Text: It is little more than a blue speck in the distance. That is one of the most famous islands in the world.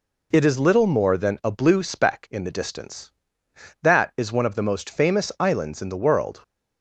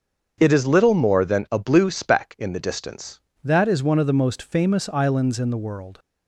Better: first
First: none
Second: starts louder than the rest; strong; until 1.3 s; 7 dB // changes voice at "That"; from 3.4 s on; 2.5 s long

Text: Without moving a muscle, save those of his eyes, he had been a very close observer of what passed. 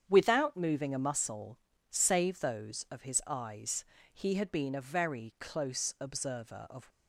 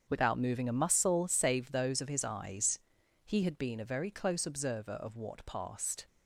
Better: second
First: starts louder than the rest; strong; until 1.0 s; 8 dB // stops before "what passed"; at 6.9 s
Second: starts louder than the rest; strong; until 1.0 s; 7.5 dB

